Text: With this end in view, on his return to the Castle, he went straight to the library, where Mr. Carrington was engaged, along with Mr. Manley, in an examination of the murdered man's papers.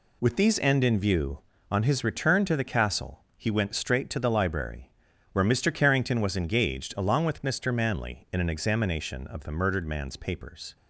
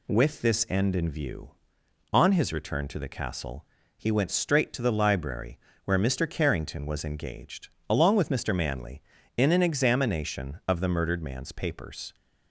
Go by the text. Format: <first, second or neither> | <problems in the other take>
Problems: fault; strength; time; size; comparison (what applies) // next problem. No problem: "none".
second | says "these" for "this"; at 0.3 s